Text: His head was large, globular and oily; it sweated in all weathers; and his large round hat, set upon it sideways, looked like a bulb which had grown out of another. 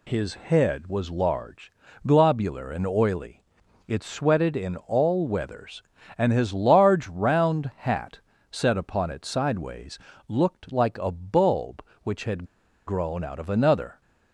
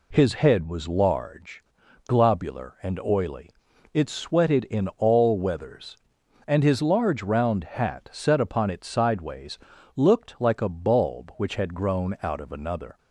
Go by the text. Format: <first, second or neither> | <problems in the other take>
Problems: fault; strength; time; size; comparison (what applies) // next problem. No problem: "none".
second | pauses between "had" and "grown"; at 12.4 s; 0.41 s long